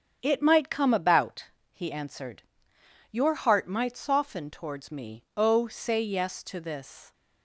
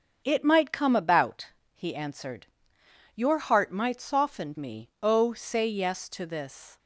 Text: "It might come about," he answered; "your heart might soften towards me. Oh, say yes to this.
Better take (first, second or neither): first